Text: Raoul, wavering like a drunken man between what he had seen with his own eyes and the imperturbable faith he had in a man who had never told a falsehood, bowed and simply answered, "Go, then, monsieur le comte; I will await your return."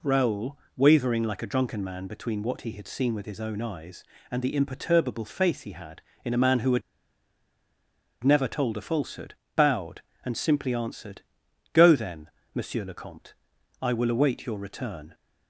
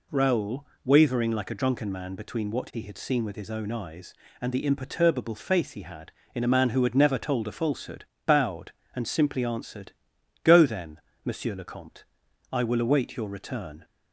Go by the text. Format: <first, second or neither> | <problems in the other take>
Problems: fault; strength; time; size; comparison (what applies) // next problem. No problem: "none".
second | pauses between "had" and "never"; strong; at 6.8 s; 1.4 s long